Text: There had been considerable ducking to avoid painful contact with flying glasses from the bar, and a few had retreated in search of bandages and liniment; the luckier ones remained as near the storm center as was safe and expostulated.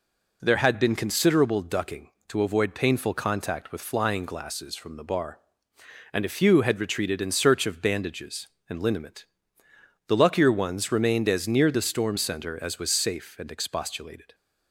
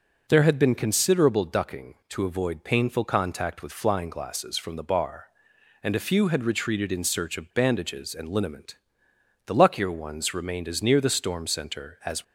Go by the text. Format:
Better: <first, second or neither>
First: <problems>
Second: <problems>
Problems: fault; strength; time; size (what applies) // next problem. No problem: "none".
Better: first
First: none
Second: stops before "was safe and expostulated"; at 12.2 s